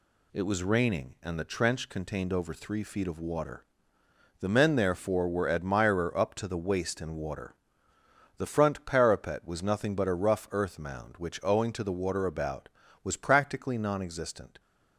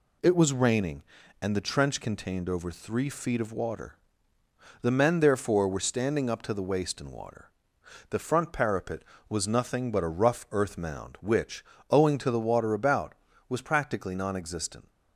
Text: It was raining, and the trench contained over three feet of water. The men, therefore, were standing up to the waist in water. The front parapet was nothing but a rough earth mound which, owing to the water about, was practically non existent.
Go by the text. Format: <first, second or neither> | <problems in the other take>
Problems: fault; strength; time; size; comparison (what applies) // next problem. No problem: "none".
second | says "admirer" for "standing"; at 5.4 s